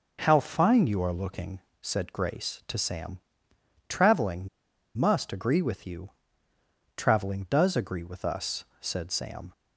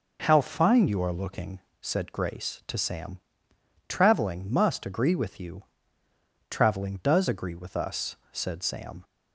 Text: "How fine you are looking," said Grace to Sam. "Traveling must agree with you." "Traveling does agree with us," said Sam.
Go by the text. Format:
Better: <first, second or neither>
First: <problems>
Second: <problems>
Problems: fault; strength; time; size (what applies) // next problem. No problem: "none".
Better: second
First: pauses between "Traveling" and "must"; noticeable; at 4.4 s; 0.49 s long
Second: none